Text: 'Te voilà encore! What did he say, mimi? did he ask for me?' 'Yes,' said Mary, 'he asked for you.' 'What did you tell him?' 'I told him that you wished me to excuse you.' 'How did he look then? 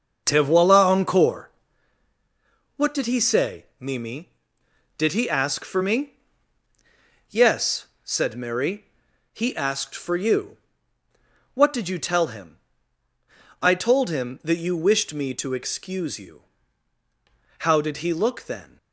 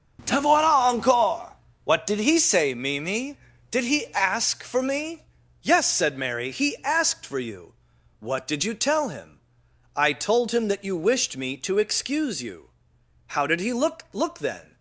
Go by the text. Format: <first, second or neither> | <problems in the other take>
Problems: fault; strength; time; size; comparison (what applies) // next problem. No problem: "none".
first | starts louder than the rest; until 1.2 s; 6.5 dB; noticeable in the first // says "look" twice; at 14.1 s